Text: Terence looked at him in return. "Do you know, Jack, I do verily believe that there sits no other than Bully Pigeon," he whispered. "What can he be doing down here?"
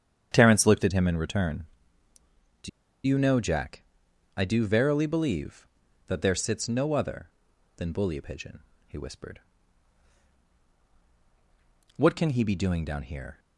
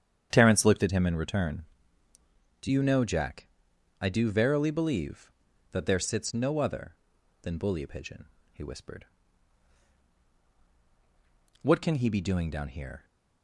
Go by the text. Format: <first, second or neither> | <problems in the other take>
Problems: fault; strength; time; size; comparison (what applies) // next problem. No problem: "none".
second | starts louder than the rest; strong; until 1.3 s; 9 dB; strong in the second // pauses between "Do" and "you"; at 2.6 s; 0.37 s long